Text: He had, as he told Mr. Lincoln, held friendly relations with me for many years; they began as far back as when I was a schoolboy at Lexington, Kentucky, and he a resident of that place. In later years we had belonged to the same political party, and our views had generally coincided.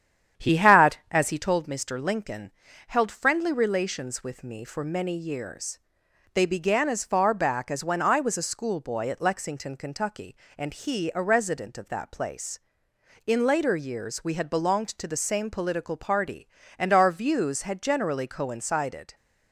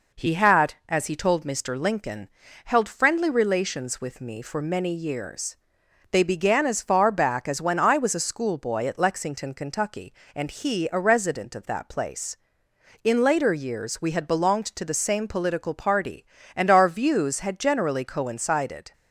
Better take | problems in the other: second | starts louder than the rest; strong; until 1.5 s; 9 dB

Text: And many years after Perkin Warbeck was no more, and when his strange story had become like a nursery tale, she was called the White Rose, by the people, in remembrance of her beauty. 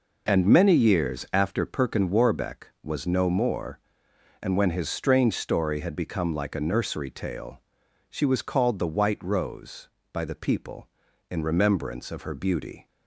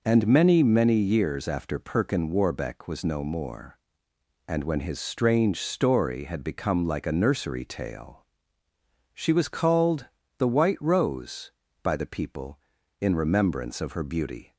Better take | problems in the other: first | says "many" twice; at 0.6 s // pauses between "called" and "the"; slight; at 10.0 s; 0.32 s long

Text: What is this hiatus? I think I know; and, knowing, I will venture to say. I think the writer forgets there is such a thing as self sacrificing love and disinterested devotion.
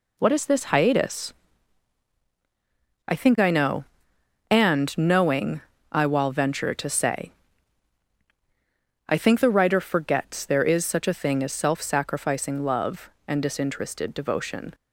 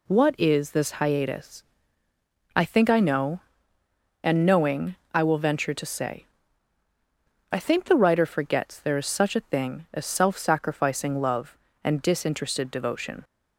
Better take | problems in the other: second | says "while" for "will"; at 6.0 s

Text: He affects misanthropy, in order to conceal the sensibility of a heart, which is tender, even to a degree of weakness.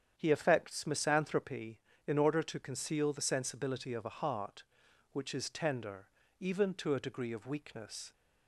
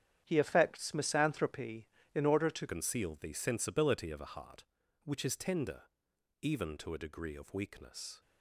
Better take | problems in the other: first | starts louder than the rest; strong; until 1.2 s; 9.5 dB; strong in the first // changes voice at "conceal"; from 2.6 s on; 5.6 s long

